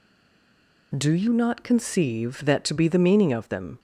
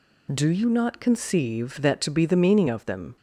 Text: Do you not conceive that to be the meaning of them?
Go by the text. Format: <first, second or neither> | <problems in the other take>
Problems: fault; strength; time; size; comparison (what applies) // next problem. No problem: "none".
second | stays silent before the first word; slight; until 0.9 s; 0.9 s long